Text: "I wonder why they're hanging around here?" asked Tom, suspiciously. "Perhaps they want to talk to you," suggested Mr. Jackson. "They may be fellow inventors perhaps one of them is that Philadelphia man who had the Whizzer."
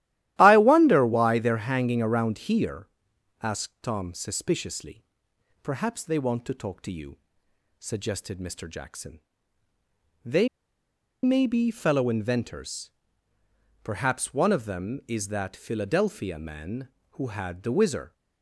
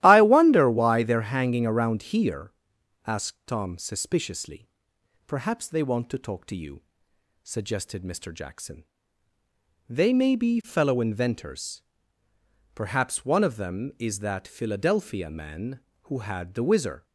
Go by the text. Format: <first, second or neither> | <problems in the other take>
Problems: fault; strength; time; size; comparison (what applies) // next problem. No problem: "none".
second | starts louder than the rest; strong; until 1.4 s; 14 dB; strong in the second // pauses between "They" and "may"; noticeable; at 10.4 s; 0.76 s long // pauses between "inventors" and "perhaps"; noticeable; at 12.9 s; 0.92 s long; noticeable in the second